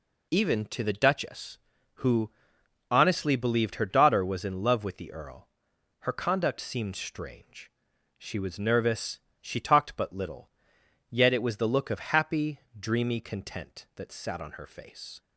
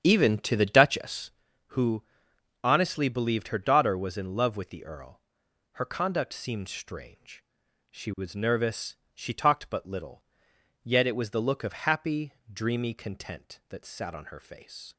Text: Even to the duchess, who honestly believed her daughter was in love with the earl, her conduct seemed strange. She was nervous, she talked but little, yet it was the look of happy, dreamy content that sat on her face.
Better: first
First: pauses between "who" and "honestly"; noticeable; at 2.3 s; 0.60 s long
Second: starts louder than the rest; strong; until 1.5 s; 9 dB // pauses between "who" and "honestly"; noticeable; at 2.0 s; 0.60 s long

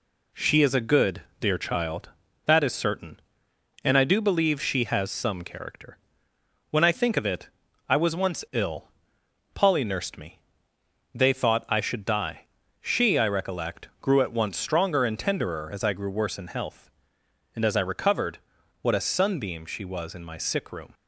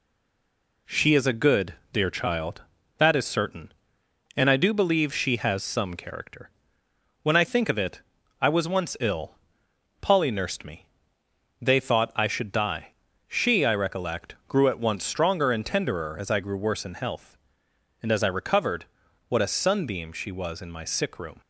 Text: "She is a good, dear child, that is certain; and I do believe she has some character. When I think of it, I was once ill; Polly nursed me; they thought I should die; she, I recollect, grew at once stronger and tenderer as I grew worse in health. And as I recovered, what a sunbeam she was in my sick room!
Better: first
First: none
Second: stays silent before the first word; slight; until 0.8 s; 0.8 s long

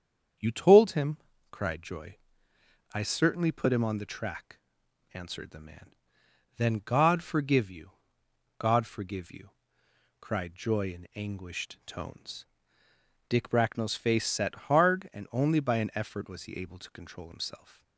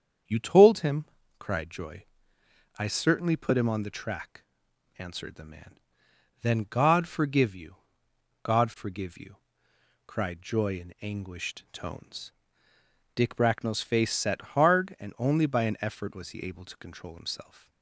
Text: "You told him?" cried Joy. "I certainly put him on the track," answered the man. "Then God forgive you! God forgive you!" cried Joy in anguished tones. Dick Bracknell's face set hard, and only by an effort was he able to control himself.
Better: neither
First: starts louder than the rest; strong; until 1.7 s; 7.5 dB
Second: starts louder than the rest; strong; until 1.6 s; 7.5 dB

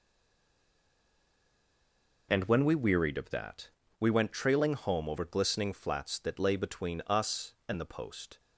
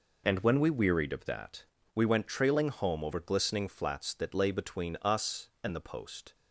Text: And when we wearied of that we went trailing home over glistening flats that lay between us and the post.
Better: second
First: stays silent before the first word; until 2.2 s; 2.2 s long // pauses between "that" and "we"; slight; at 3.6 s; 0.30 s long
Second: pauses between "that" and "we"; slight; at 1.6 s; 0.30 s long

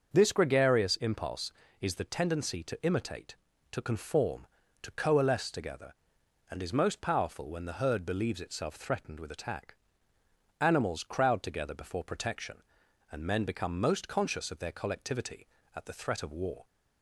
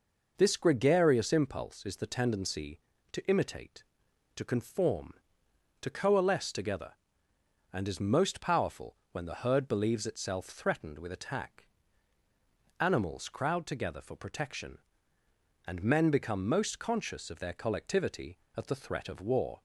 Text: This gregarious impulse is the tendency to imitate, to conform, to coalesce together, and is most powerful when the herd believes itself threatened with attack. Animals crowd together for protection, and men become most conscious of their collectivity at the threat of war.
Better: second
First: starts louder than the rest; until 1.1 s; 6.5 dB // says "before" for "for"; at 11.7 s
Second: none

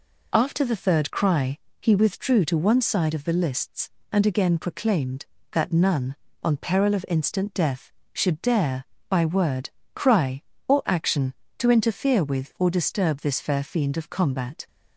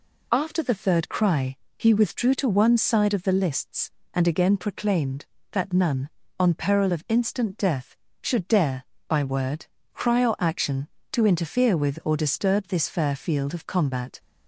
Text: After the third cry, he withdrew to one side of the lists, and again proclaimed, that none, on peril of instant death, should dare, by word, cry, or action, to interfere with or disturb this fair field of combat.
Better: second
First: says "fiend" for "field"; at 13.6 s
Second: none

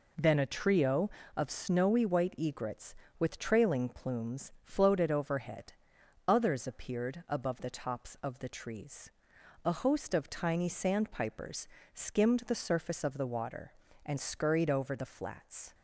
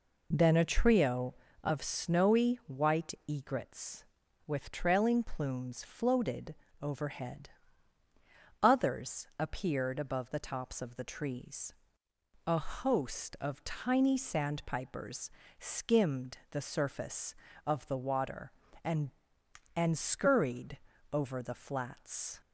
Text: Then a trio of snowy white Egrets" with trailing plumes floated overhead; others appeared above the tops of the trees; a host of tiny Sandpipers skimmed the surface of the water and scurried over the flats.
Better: first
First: pauses between "Sandpipers" and "skimmed"; slight; at 11.6 s; 0.24 s long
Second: pauses between "floated" and "overhead"; slight; at 6.5 s; 0.26 s long // pauses between "Sandpipers" and "skimmed"; slight; at 15.2 s; 0.30 s long // says "and" twice; at 19.7 s // pauses between "scurried" and "over"; slight; at 20.7 s; 0.34 s long

